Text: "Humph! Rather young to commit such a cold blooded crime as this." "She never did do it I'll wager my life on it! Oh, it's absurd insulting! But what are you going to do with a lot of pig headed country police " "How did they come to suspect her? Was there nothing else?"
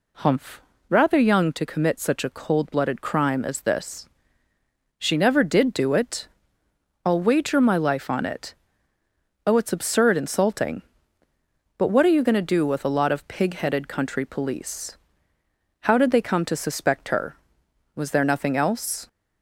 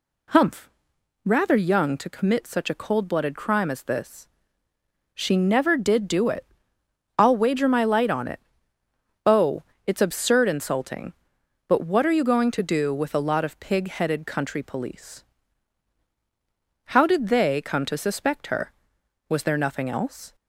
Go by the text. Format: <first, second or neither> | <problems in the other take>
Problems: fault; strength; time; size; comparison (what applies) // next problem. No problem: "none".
first | pauses between "it" and "I'll"; noticeable; at 6.4 s; 0.72 s long; noticeable in the first // says "light" for "life"; at 7.8 s